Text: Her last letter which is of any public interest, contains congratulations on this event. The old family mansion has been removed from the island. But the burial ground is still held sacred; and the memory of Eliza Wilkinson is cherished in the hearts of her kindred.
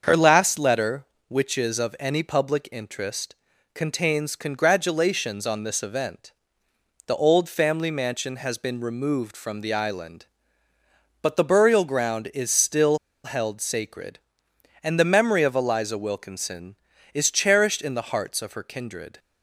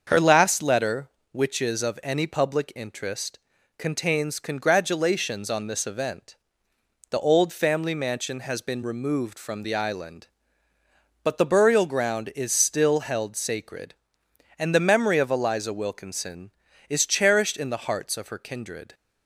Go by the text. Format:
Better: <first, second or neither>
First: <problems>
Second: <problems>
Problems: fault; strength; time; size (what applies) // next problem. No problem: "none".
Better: second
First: starts louder than the rest; until 1.0 s; 7 dB // pauses between "still" and "held"; slight; at 12.9 s; 0.26 s long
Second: starts louder than the rest; until 1.0 s; 7 dB